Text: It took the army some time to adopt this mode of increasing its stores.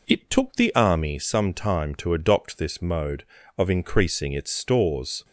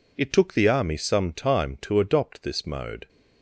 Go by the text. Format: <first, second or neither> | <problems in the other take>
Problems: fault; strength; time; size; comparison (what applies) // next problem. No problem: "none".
first | stops before "of increasing its stores"; at 3.0 s